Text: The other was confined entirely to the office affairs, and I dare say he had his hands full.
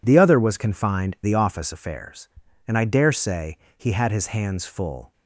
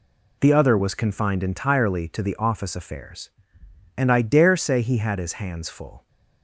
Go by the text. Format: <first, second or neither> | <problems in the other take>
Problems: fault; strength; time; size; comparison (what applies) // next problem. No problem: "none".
second | skips "entirely to"; at 1.1 s // pauses between "say" and "he"; slight; at 3.5 s; 0.18 s long